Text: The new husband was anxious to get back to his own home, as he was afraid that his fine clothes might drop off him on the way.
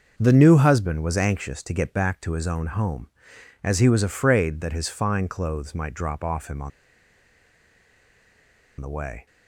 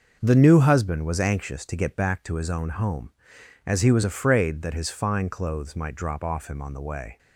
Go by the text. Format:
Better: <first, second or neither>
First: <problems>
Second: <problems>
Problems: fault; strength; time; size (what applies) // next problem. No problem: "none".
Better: second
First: starts louder than the rest; noticeable; until 1.1 s; 6 dB // pauses between "on" and "the"; strong; at 6.7 s; 2.0 s long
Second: starts louder than the rest; noticeable; until 1.2 s; 6 dB